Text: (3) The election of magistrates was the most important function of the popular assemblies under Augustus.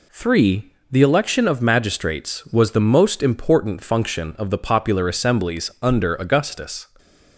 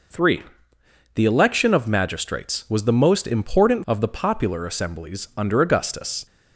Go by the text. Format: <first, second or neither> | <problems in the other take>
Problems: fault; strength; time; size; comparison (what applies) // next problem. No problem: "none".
first | skips "function"; at 3.8 s